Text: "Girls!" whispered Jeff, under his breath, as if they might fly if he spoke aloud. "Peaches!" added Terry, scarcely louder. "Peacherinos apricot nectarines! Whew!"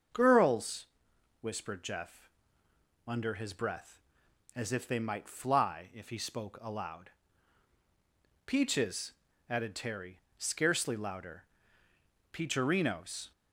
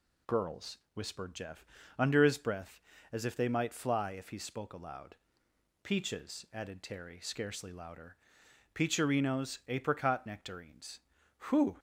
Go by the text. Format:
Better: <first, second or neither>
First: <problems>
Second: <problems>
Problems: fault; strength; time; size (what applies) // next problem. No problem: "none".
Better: second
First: starts louder than the rest; until 1.7 s; 6.5 dB // stops before "apricot nectarines Whew"; at 13.3 s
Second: none